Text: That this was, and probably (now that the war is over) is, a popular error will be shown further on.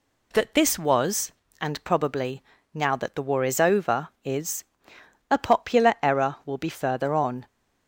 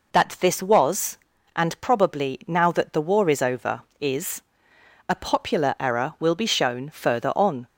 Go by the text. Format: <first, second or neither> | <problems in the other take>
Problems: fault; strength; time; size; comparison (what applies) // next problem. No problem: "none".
second | skips "shown"; at 6.6 s